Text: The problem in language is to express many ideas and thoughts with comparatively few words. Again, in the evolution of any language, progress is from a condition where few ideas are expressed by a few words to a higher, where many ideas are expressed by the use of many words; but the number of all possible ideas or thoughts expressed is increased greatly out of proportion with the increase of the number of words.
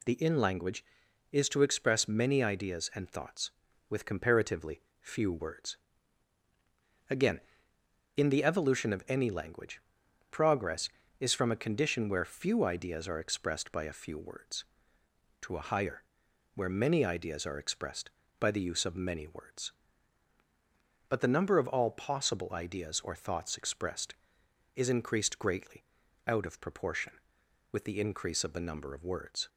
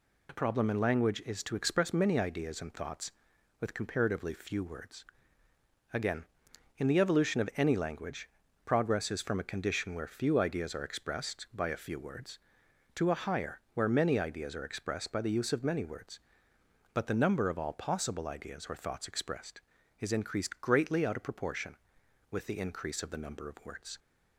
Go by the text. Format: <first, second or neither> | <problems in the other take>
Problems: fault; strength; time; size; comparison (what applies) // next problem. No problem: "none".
second | skips "problem"; at 0.1 s // pauses between "comparatively" and "few"; slight; at 4.8 s; 0.18 s long // pauses between "greatly" and "out"; at 25.8 s; 0.42 s long